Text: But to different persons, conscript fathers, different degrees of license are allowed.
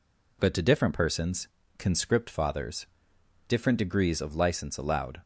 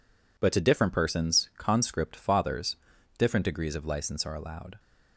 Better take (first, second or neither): second